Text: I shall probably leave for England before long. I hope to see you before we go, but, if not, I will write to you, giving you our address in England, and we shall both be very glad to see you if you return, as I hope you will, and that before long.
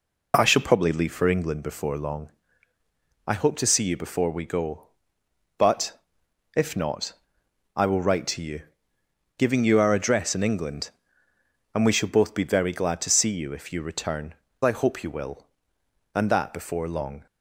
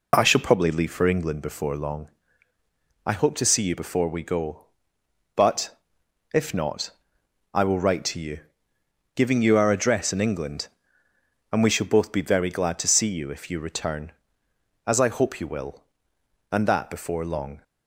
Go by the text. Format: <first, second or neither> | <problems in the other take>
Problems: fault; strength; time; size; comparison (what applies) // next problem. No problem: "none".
second | skips "as"; at 14.4 s